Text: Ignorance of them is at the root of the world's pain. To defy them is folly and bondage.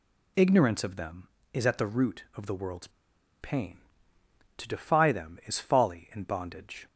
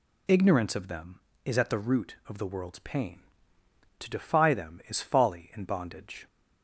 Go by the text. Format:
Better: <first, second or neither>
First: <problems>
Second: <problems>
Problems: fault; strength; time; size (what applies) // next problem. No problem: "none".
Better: second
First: pauses between "world's" and "pain"; noticeable; at 2.8 s; 0.52 s long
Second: none